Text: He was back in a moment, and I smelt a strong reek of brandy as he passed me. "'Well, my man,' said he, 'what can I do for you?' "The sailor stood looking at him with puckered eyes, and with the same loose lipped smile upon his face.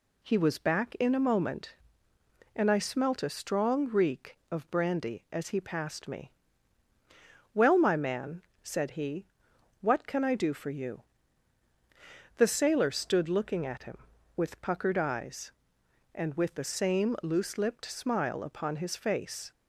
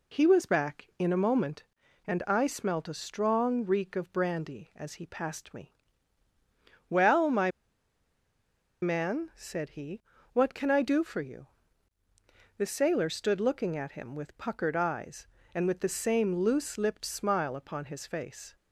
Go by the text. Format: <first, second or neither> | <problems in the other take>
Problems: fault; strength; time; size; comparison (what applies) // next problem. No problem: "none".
first | pauses between "my" and "man"; strong; at 7.5 s; 1.3 s long